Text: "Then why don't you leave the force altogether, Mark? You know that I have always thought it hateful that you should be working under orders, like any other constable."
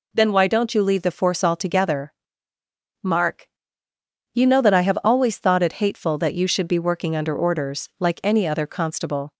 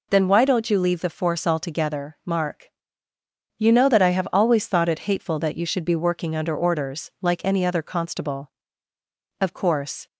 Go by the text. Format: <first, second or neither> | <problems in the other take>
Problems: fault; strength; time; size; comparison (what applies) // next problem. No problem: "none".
first | goes on to say "Of course"; noticeable; from 9.4 s on; 0.66 s long